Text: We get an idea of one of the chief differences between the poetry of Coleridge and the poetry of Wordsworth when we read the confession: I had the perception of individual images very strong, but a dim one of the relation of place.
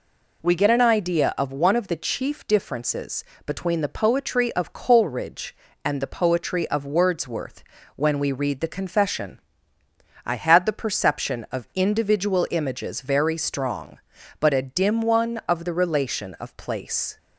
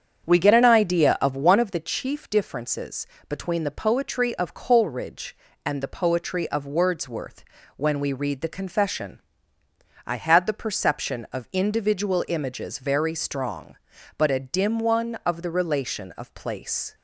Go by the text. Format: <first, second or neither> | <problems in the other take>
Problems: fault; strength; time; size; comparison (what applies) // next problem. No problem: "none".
first | starts louder than the rest; strong; until 1.8 s; 8 dB // pauses between "differences" and "between"; slight; at 3.0 s; 0.20 s long; slight in the first // pauses between "Wordsworth" and "when"; slight; at 7.4 s; 0.34 s long; slight in the first